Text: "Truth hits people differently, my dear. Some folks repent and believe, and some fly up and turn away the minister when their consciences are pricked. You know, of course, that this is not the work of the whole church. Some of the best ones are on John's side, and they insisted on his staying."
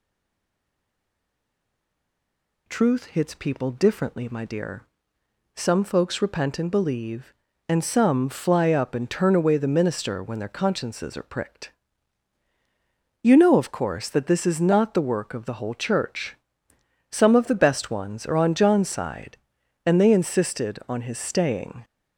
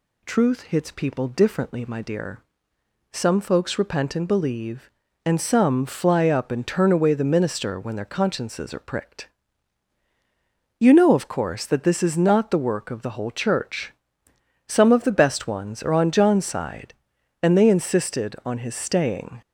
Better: second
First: stays silent before the first word; strong; until 2.6 s; 2.6 s long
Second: none

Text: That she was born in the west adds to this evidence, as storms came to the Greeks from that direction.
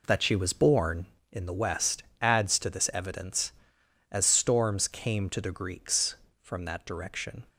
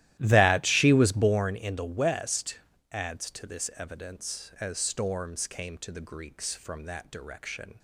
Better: first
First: pauses between "west" and "adds"; slight; at 2.0 s; 0.18 s long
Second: starts louder than the rest; strong; until 1.6 s; 14 dB // pauses between "west" and "adds"; slight; at 2.5 s; 0.32 s long

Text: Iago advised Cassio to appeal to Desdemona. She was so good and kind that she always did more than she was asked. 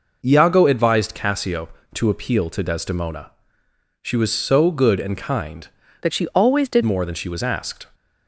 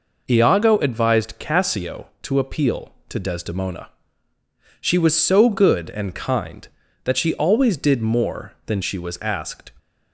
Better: second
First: changes voice from "that" to "did"; from 6.0 to 6.8 s; 0.8 s long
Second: none

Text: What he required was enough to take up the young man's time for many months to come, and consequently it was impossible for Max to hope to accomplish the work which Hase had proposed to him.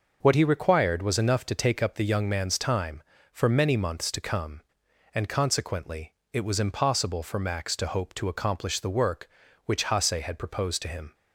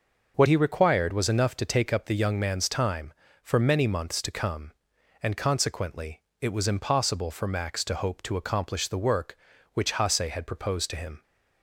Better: neither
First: pauses between "consequently" and "it"; slight; at 6.1 s; 0.18 s long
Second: pauses between "consequently" and "it"; slight; at 6.2 s; 0.18 s long

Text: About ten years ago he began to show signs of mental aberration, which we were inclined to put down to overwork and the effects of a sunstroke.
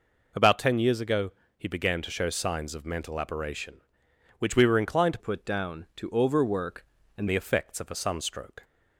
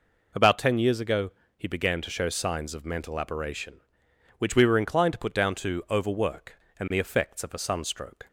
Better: second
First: pauses between "ago" and "he"; slight; at 1.3 s; 0.26 s long // changes voice from "put" to "and"; from 5.1 to 7.2 s; 2.1 s long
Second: pauses between "ago" and "he"; slight; at 1.3 s; 0.26 s long

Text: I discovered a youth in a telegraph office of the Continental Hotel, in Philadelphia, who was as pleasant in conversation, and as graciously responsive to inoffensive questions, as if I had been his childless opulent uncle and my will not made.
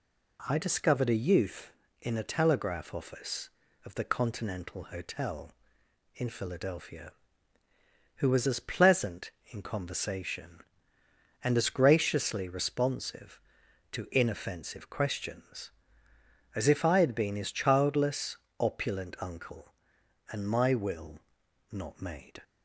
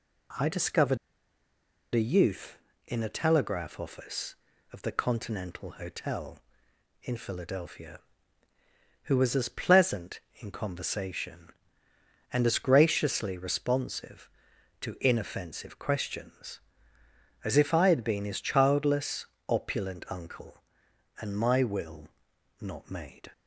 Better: first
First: pauses between "childless" and "opulent"; slight; at 18.3 s; 0.22 s long // pauses between "will" and "not"; noticeable; at 21.1 s; 0.52 s long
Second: pauses between "discovered" and "a"; noticeable; at 0.9 s; 0.96 s long // pauses between "childless" and "opulent"; slight; at 19.2 s; 0.22 s long // pauses between "will" and "not"; noticeable; at 22.0 s; 0.52 s long

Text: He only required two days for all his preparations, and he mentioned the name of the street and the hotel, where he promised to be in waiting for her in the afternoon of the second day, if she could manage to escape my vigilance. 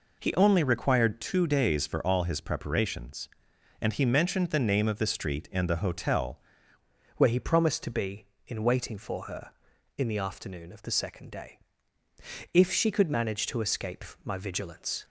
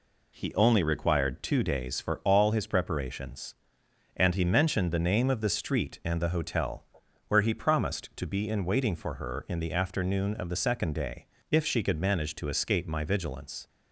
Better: second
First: changes voice at "where"; from 7.1 s on; 7.9 s long // pauses between "escape" and "my"; slight; at 14.0 s; 0.22 s long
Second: none

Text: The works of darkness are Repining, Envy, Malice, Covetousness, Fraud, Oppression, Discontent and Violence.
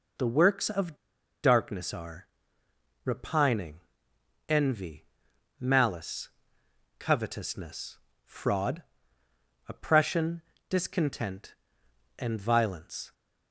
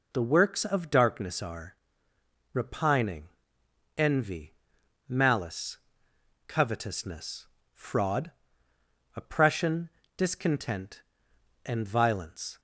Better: second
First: pauses between "of" and "darkness"; noticeable; at 0.9 s; 0.49 s long // pauses between "are" and "Repining"; noticeable; at 2.2 s; 0.76 s long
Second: pauses between "are" and "Repining"; noticeable; at 1.7 s; 0.76 s long

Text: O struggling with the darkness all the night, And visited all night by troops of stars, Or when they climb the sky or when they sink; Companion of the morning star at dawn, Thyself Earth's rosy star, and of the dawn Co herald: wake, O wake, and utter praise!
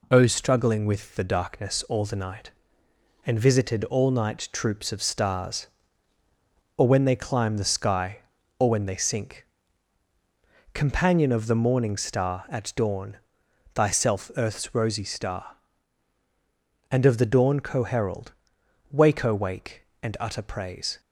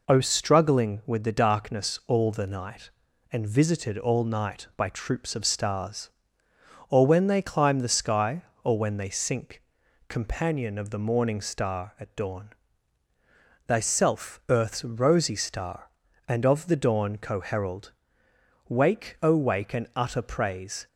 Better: second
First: skips "by"; at 4.5 s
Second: none

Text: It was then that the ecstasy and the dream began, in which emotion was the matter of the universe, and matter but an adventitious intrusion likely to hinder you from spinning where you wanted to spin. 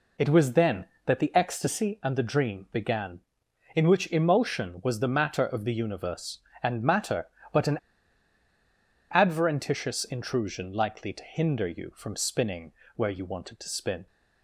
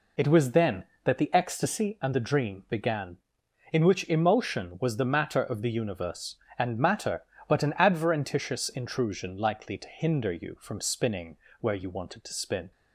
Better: second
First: pauses between "an" and "adventitious"; strong; at 7.7 s; 1.3 s long // pauses between "spinning" and "where"; slight; at 12.7 s; 0.24 s long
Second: pauses between "spinning" and "where"; slight; at 11.3 s; 0.24 s long

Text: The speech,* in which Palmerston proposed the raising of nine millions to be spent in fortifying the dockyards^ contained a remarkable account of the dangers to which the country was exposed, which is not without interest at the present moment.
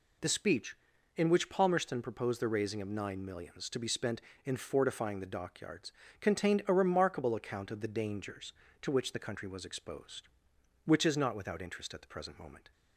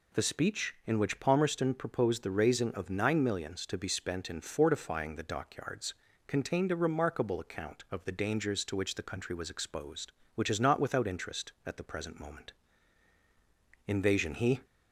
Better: first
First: pauses between "dockyards" and "contained"; slight; at 5.9 s; 0.30 s long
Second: pauses between "dockyards" and "contained"; slight; at 5.9 s; 0.34 s long // goes on to say "Invasion he"; noticeable; from 13.8 s on; 0.76 s long

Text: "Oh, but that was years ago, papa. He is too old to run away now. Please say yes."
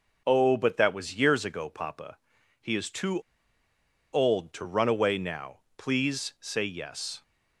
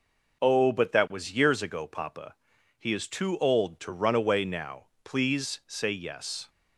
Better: second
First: pauses between "too" and "old"; noticeable; at 3.1 s; 0.93 s long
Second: none

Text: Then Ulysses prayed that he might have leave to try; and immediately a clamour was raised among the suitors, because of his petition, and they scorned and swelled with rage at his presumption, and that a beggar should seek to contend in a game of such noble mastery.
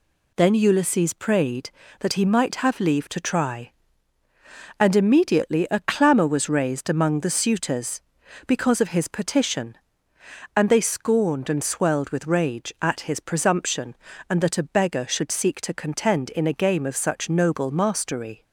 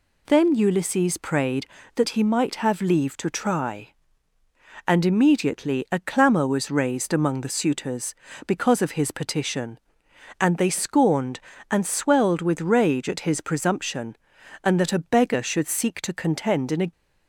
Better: first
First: none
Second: stops before "game of such noble mastery"; at 16.9 s

